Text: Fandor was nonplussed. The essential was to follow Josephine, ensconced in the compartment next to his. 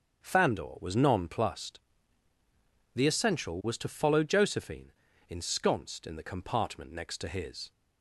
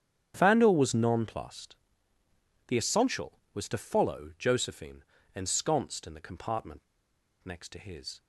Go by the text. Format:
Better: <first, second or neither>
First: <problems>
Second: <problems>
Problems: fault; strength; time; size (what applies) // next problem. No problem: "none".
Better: first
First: starts louder than the rest; until 1.2 s; 7 dB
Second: starts louder than the rest; strong; until 1.3 s; 8.5 dB // pauses between "compartment" and "next"; noticeable; at 6.8 s; 0.64 s long